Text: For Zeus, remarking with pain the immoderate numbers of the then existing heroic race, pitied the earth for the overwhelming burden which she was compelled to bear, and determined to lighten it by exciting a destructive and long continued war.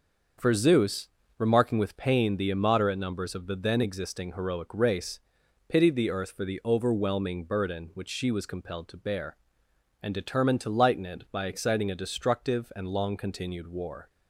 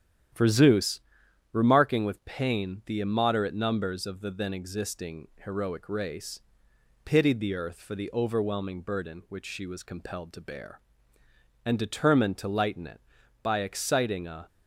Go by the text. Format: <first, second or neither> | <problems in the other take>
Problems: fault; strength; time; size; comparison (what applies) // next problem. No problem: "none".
first | starts louder than the rest; strong; until 1.8 s; 10 dB; also in the first // pauses between "existing" and "heroic"; slight; at 5.2 s; 0.18 s long // stops before "destructive and long continued war"; at 14.4 s